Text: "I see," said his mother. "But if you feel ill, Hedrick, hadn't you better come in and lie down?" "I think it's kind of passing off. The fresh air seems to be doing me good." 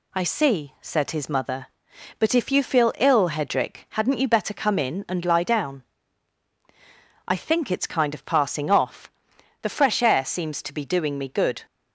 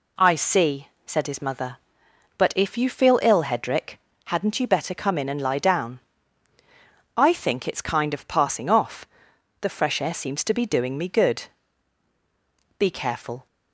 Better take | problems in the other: first | goes on to say "Be careful"; noticeable; from 12.7 s on; 0.68 s long

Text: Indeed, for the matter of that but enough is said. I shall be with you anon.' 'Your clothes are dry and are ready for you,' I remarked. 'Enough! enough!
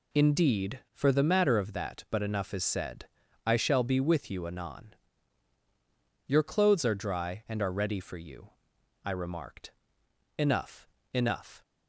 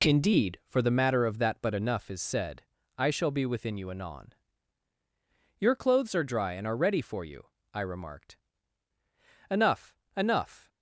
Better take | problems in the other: first | says "within" for "with"; at 3.4 s

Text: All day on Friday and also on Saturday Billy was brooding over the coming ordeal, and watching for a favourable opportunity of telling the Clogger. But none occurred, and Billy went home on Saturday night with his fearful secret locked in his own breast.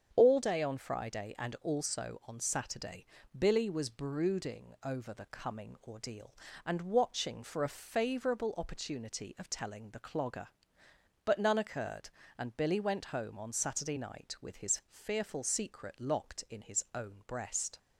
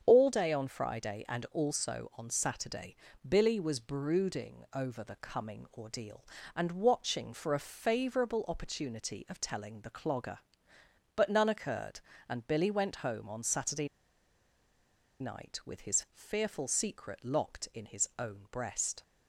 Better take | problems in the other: first | starts louder than the rest; strong; until 1.0 s; 8 dB; strong in the first // pauses between "Saturday" and "Billy"; slight; at 2.9 s; 0.32 s long; slight in the first // pauses between "Saturday" and "night"; strong; at 13.8 s; 1.3 s long

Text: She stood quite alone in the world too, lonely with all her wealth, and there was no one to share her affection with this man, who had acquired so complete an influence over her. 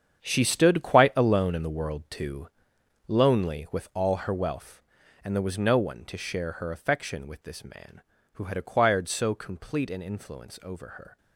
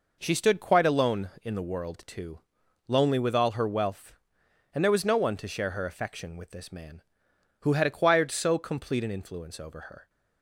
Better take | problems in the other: second | gets quieter; strong; throughout; 13.5 dB

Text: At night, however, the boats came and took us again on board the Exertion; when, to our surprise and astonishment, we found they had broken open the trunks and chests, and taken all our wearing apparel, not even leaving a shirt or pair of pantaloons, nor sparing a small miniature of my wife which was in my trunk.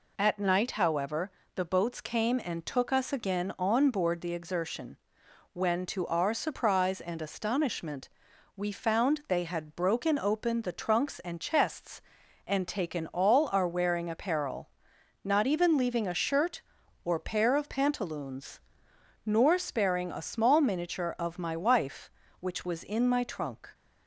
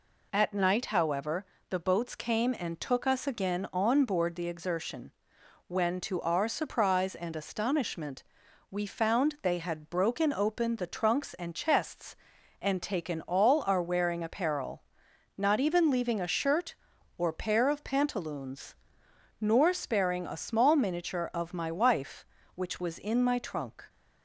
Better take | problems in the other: neither | none

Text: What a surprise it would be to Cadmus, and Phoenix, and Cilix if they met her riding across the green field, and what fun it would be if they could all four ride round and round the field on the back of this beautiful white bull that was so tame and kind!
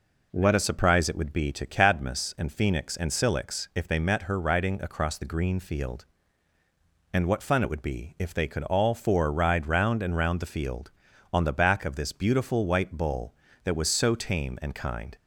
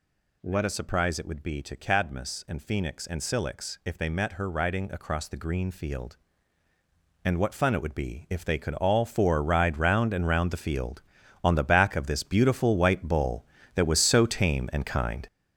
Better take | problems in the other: first | gets louder; strong; throughout; 8 dB

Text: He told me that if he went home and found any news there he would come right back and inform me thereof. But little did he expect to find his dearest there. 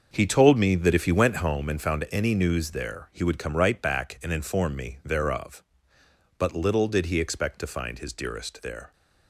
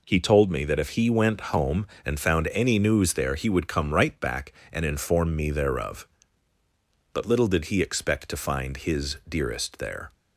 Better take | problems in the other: second | starts louder than the rest; until 1.5 s; 6.5 dB

